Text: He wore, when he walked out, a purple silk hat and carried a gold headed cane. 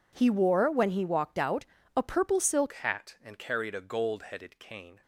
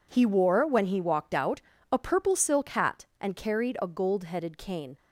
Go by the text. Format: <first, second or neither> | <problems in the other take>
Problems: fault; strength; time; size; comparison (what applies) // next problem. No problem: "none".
second | changes voice at "hat"; from 2.7 s on; 2.3 s long